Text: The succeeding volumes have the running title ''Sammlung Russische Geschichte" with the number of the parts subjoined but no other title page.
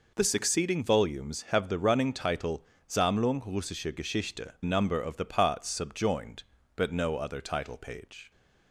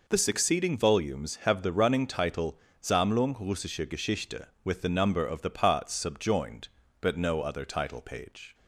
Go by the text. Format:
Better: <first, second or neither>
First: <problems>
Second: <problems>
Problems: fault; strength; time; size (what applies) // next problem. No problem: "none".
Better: second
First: pauses between "title" and "Sammlung"; slight; at 2.6 s; 0.20 s long // skips "with the"; at 4.5 s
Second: pauses between "title" and "Sammlung"; slight; at 2.5 s; 0.20 s long